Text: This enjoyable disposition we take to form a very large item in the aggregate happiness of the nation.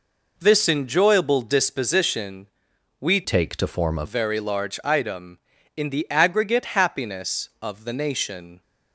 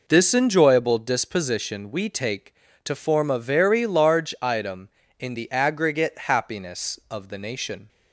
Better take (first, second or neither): second